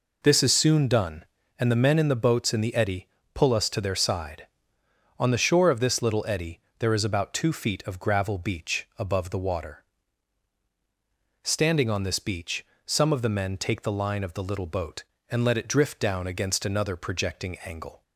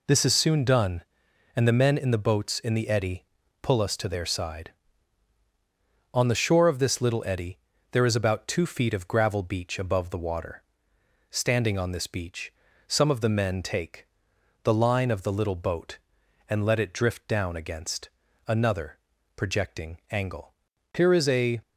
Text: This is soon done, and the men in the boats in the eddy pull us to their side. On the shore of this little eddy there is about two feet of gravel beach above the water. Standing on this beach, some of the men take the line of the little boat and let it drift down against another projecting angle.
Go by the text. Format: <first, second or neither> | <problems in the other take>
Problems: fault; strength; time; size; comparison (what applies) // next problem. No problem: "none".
first | pauses between "eddy" and "pull"; slight; at 3.2 s; 0.36 s long; slight in the first // pauses between "eddy" and "there"; slight; at 7.5 s; 0.32 s long; slight in the first // pauses between "take" and "the"; noticeable; at 14.0 s; 0.56 s long // pauses between "against" and "another"; at 18.0 s; 0.38 s long // pauses between "another" and "projecting"; at 18.9 s; 0.38 s long // goes on to say "Here is a"; noticeable; from 20.9 s on; 0.68 s long